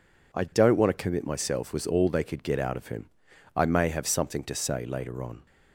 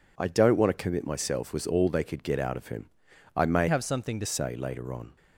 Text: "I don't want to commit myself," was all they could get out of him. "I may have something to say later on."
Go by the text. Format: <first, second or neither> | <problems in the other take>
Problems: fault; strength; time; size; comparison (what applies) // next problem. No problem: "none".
first | changes voice from "have" to "to"; from 3.6 to 4.2 s; 0.6 s long